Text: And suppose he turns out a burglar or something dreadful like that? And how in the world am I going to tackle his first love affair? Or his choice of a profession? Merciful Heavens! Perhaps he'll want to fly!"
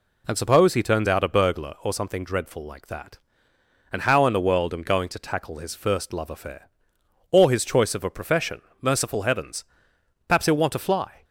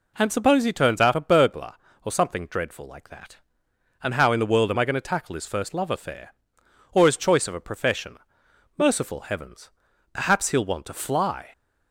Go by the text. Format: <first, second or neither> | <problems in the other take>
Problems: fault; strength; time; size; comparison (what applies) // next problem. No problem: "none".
second | skips "I"; at 4.8 s